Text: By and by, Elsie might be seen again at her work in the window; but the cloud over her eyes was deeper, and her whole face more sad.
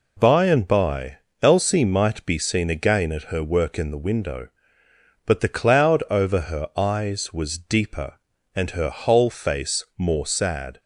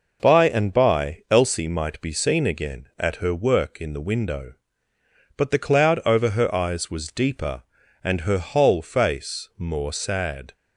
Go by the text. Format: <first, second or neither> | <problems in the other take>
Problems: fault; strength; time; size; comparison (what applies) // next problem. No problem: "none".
neither | none